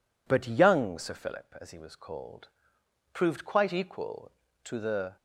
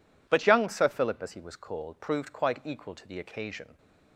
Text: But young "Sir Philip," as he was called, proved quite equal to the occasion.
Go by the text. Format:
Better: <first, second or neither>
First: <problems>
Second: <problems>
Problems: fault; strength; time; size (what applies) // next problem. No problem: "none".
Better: second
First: stops before "occasion"; at 5.1 s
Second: none